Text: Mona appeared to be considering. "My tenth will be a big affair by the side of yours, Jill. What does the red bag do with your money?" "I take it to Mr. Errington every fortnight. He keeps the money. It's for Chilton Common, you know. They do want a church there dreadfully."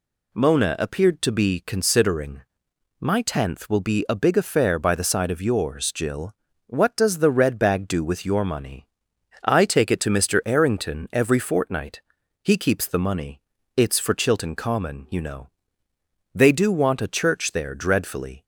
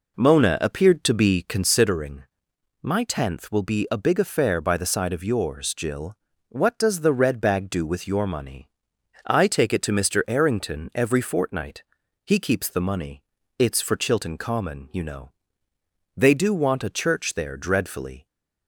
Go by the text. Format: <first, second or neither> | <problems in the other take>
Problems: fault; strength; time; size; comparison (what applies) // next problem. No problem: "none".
first | starts louder than the rest; noticeable; until 1.9 s; 4 dB